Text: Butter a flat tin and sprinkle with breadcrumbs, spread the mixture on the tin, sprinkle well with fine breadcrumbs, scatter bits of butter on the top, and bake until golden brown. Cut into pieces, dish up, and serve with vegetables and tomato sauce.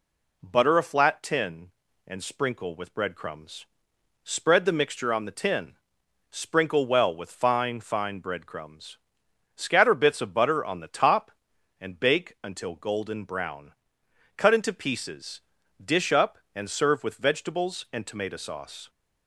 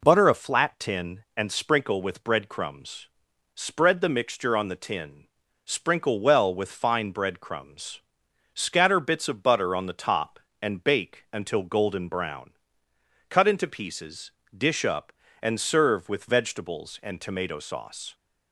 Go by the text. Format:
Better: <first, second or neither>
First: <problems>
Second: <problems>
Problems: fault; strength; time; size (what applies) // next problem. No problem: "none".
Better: second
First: says "fine" twice; at 7.7 s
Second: none